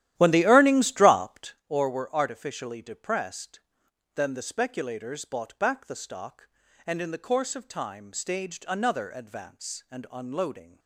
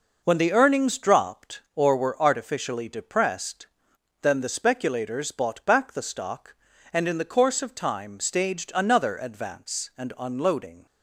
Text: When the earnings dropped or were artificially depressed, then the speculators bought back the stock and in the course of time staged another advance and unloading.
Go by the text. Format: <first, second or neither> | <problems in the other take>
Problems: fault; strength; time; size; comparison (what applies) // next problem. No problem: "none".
second | starts louder than the rest; strong; until 1.6 s; 13 dB